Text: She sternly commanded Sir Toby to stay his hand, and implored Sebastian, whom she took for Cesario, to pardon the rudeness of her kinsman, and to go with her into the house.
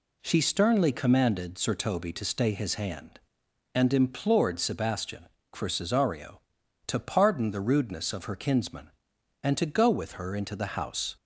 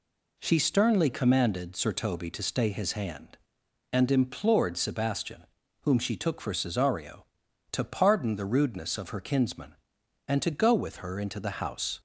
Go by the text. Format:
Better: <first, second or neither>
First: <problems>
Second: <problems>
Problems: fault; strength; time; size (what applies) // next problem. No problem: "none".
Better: second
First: skips "whom she took"; at 5.4 s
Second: none